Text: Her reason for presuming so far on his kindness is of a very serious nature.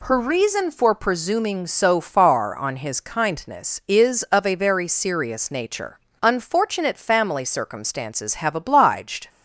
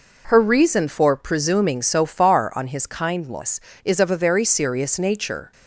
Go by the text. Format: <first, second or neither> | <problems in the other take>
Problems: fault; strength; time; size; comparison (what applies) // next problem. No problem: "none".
second | goes on to say "Unfortunate family circumstances have obliged"; strong; from 6.2 s on; 3.0 s long